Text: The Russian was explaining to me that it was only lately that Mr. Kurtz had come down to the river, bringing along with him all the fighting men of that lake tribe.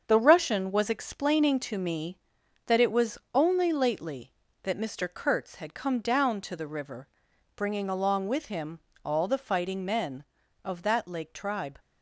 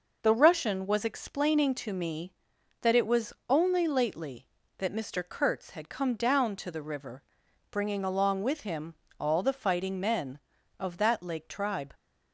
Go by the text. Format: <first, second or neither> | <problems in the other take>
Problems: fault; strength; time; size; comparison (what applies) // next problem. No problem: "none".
second | gets quieter; throughout; 7 dB // pauses between "was" and "only"; slight; at 3.1 s; 0.16 s long; slight in the second // pauses between "him" and "all"; slight; at 8.8 s; 0.22 s long; slight in the second